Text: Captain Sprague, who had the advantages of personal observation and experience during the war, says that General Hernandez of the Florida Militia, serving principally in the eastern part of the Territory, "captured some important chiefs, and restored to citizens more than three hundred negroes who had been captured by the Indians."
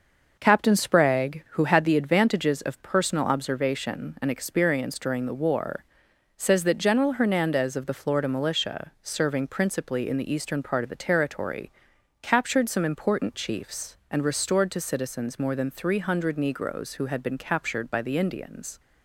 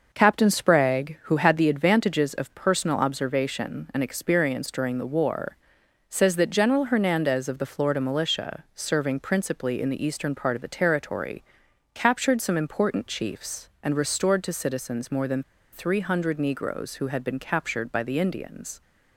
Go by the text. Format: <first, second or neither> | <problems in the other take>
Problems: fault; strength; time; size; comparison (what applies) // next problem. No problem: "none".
first | pauses between "than" and "three"; slight; at 15.4 s; 0.30 s long